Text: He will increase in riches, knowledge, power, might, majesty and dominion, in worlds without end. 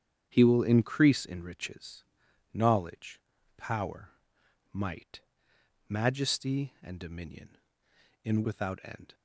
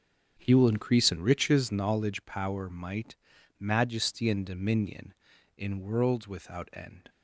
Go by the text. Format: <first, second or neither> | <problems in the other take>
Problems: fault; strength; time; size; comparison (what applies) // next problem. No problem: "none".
second | starts louder than the rest; strong; until 1.2 s; 8.5 dB; also in the second // skips "worlds"; at 8.4 s